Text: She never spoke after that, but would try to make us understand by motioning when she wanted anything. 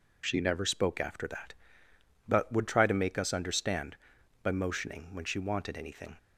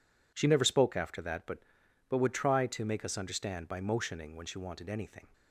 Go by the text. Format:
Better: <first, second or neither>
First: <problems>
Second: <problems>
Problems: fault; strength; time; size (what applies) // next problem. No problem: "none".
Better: first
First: none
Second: says "but" twice; at 2.0 s